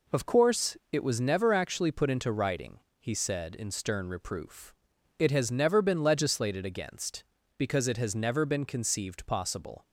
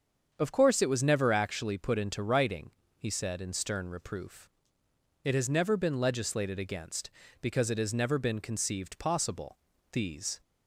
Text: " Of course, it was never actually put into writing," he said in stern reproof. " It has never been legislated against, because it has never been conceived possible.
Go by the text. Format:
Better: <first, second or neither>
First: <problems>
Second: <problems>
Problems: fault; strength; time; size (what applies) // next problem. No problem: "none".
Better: first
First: none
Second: starts louder than the rest; until 1.3 s; 7 dB // goes on to say "These"; slight; from 9.9 s on; 0.48 s long